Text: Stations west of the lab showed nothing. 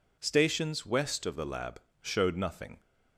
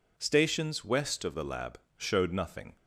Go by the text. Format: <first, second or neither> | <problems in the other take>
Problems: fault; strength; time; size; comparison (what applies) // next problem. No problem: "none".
neither | pauses between "lab" and "showed"; slight; the same in both